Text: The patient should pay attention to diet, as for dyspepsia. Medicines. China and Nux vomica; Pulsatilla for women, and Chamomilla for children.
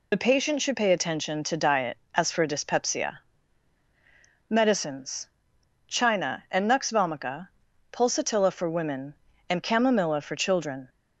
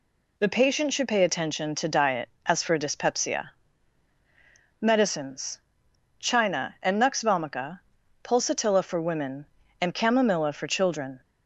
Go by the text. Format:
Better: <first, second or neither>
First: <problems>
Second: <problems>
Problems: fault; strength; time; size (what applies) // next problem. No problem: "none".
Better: second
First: loses the start of "The"; at 0.1 s; 55 ms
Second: none